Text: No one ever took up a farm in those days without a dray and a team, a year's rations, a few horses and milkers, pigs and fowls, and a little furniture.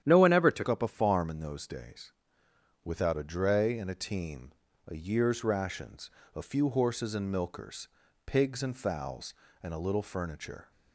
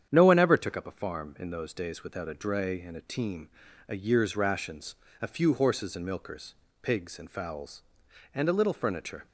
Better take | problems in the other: second | starts louder than the rest; strong; until 1.0 s; 10 dB; strong in the second // changes voice at "up"; from 0.6 s on; 10.1 s long // pauses between "days" and "without"; noticeable; at 2.1 s; 0.72 s long

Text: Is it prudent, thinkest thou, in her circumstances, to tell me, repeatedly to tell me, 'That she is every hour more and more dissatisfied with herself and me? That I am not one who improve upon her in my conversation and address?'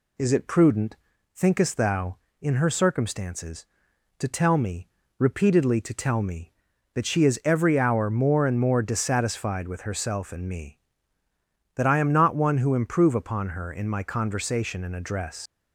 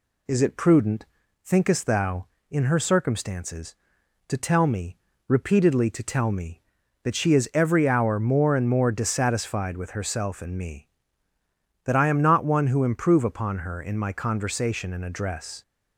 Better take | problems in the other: second | leaves "address" unfinished; at 15.4 s; 70 ms

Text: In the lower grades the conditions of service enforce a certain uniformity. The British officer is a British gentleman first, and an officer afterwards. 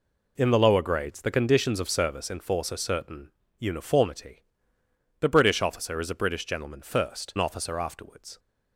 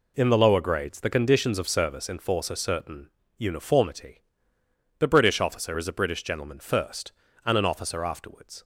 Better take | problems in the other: second | pauses between "certain" and "uniformity"; slight; at 3.3 s; 0.28 s long; slight in the second // skips "and"; at 7.3 s

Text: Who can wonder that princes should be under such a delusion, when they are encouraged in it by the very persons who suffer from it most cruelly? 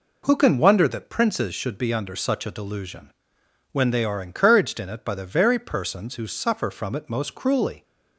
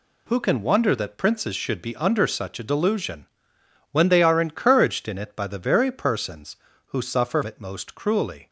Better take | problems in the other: first | skips "from"; at 7.4 s

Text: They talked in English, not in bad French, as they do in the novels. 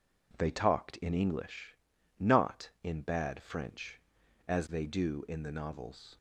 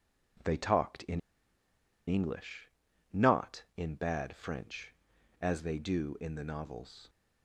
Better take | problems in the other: first | pauses between "in" and "English"; noticeable; at 1.1 s; 0.87 s long

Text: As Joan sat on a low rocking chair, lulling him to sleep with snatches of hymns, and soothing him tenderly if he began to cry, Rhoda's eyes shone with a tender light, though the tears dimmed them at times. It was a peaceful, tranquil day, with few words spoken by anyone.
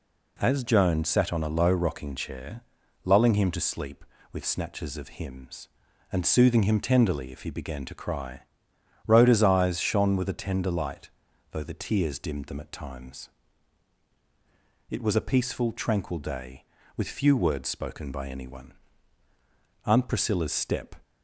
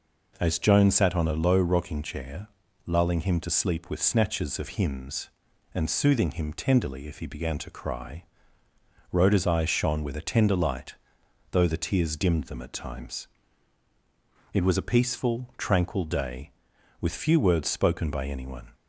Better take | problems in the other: second | goes on to say "Aunt Priscilla's step"; noticeable; from 19.8 s on; 1.1 s long

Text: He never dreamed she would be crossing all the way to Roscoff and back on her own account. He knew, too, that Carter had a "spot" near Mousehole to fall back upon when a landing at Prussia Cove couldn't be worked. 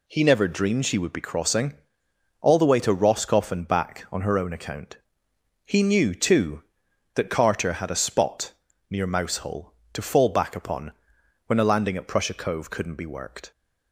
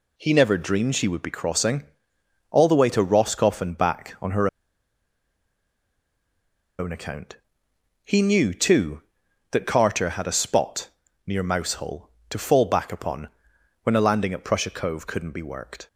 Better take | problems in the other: first | pauses between "crossing" and "all"; noticeable; at 1.8 s; 0.66 s long; noticeable in the first // pauses between "her" and "own"; strong; at 4.4 s; 2.3 s long // pauses between "spot" and "near"; slight; at 10.8 s; 0.36 s long; slight in the first // pauses between "upon" and "when"; noticeable; at 13.2 s; 0.52 s long; noticeable in the first

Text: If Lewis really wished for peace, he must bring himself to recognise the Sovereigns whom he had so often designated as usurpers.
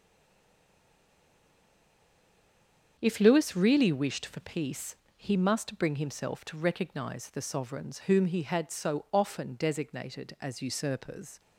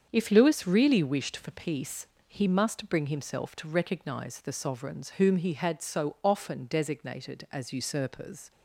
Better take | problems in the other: second | stays silent before the first word; strong; until 2.9 s; 2.9 s long // starts louder than the rest; strong; until 4.0 s; 7.5 dB; strong in the second

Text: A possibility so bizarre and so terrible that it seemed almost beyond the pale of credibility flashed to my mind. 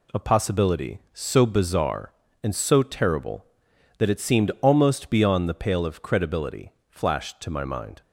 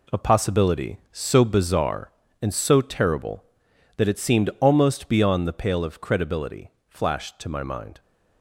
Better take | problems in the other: first | gets quieter; strong; throughout; 9 dB // pauses between "credibility" and "flashed"; slight; at 6.7 s; 0.18 s long; slight in the first

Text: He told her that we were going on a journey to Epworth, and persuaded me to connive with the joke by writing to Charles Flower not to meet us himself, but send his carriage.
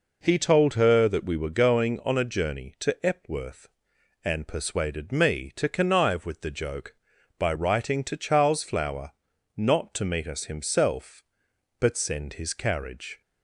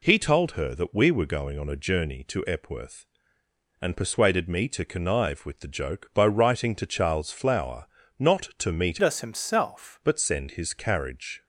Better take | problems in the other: first | pauses between "Flower" and "not"; slight; at 7.8 s; 0.32 s long; also in the first // changes voice from "us" to "himself"; from 9.0 to 9.9 s; 0.9 s long

